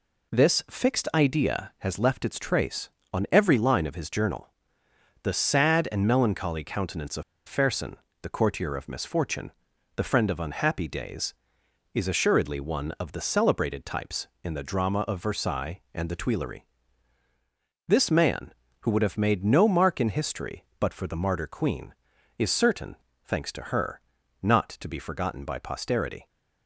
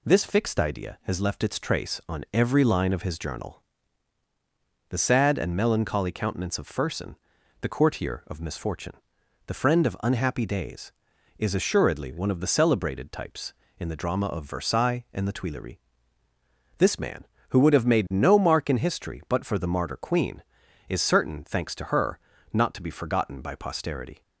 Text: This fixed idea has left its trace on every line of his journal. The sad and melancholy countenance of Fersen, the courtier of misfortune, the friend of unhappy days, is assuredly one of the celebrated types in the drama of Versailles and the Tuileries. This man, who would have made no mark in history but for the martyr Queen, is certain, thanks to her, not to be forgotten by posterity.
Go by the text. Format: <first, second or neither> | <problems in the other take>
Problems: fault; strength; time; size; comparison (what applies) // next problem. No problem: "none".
second | pauses between "of" and "Fersen"; slight; at 7.2 s; 0.25 s long